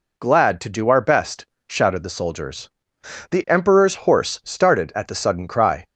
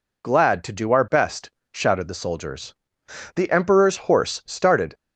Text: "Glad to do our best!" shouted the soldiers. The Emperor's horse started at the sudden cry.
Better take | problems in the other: first | stops before "at the sudden cry"; at 4.9 s

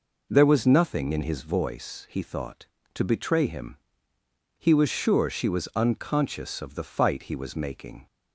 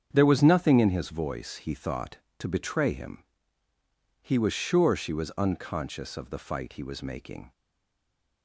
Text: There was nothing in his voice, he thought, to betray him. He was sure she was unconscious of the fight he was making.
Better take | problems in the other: first | starts louder than the rest; strong; until 1.1 s; 7.5 dB // stays silent after the last word; slight; from 7.5 s on; 0.9 s long

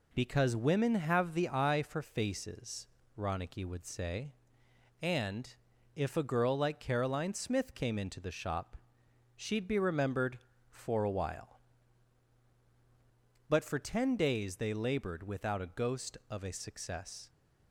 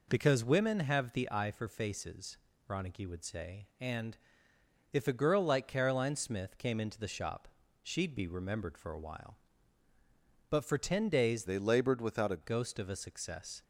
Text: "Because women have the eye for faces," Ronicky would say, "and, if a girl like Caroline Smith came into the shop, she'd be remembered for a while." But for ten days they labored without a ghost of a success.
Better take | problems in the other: first | changes voice from "they" to "a"; from 11.4 to 12.4 s; 1.0 s long

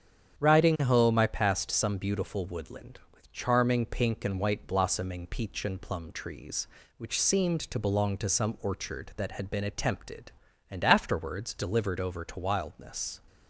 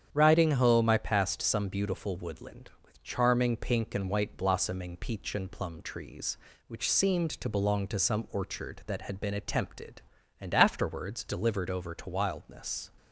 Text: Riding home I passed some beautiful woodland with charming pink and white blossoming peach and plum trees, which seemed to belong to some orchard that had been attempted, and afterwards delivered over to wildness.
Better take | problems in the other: neither | starts louder than the rest; strong; the same in both

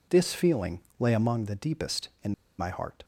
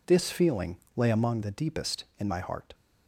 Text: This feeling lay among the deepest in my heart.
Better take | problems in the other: second | pauses between "feeling" and "lay"; slight; at 0.7 s; 0.20 s long; slight in the second // pauses between "in" and "my"; slight; at 2.3 s; 0.26 s long

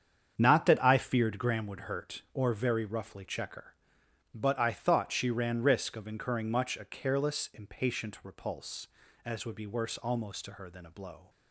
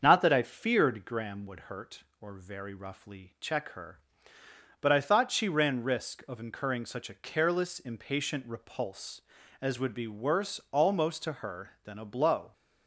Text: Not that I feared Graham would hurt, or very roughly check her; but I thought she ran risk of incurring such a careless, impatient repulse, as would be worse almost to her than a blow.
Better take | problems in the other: second | starts louder than the rest; strong; until 1.3 s; 7.5 dB; also in the second // says "much" for "such"; at 6.5 s

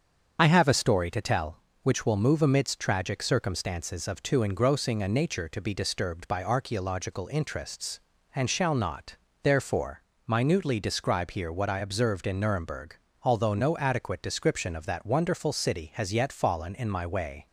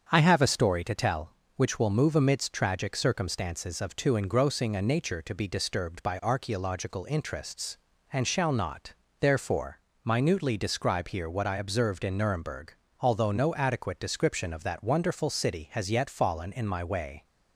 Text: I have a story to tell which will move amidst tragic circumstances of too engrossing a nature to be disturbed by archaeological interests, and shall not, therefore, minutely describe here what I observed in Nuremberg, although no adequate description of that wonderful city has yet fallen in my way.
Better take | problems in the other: second | loses the start of "I"; at 0.3 s; 65 ms // starts louder than the rest; strong; until 1.4 s; 7 dB; strong in the second

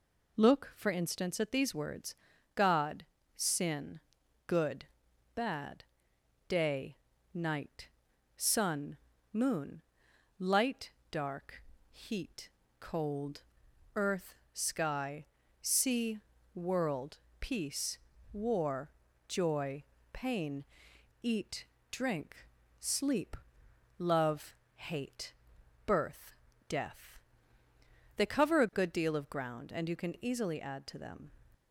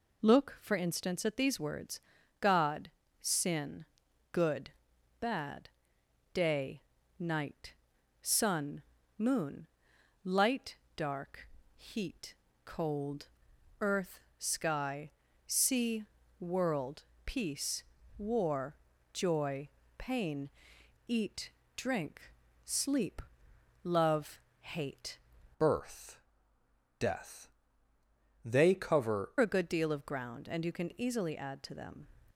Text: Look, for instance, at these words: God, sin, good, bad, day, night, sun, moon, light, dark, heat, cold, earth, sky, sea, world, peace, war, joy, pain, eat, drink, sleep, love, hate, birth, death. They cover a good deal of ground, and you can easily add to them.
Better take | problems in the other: first | changes voice from "birth" to "cover"; from 25.5 to 29.3 s; 3.8 s long

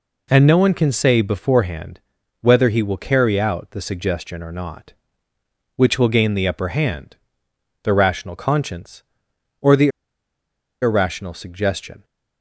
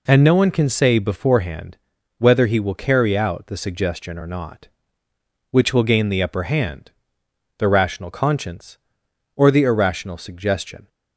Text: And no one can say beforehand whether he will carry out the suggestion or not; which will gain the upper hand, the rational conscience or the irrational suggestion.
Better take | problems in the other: second | pauses between "beforehand" and "whether"; at 1.9 s; 0.42 s long; also in the second // pauses between "the" and "irrational"; noticeable; at 9.8 s; 0.92 s long

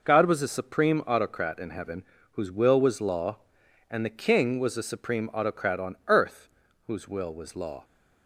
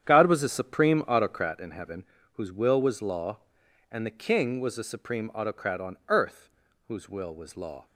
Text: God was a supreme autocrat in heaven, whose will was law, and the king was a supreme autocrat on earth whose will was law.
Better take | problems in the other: first | starts louder than the rest; strong; until 1.6 s; 9 dB // pauses between "earth" and "whose"; at 6.4 s; 0.38 s long; also in the first

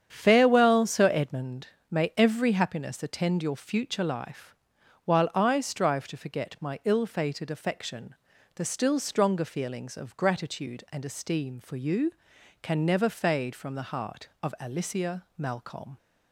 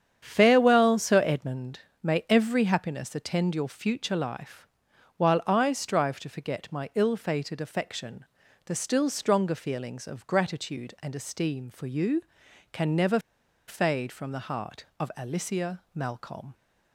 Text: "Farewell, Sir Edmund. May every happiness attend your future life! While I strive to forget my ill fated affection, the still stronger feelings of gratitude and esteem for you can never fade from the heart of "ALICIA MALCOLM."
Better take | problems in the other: first | starts louder than the rest; strong; until 1.2 s; 8.5 dB; strong in the first // pauses between "never" and "fade"; noticeable; at 13.1 s; 0.48 s long

